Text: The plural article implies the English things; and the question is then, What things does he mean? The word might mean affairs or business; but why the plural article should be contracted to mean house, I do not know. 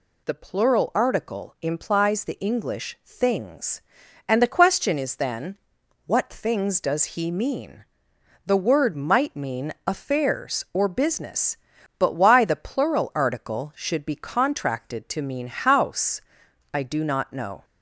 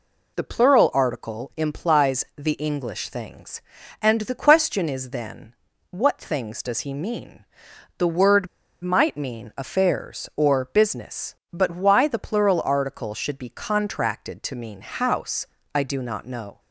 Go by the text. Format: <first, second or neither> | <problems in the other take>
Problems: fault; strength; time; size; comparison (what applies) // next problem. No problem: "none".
first | pauses between "word" and "might"; at 8.4 s; 0.36 s long